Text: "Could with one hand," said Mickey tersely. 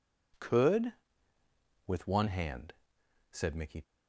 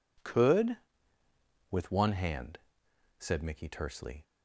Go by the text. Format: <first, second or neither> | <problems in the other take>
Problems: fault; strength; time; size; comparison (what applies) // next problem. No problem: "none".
second | stops before "tersely"; at 3.8 s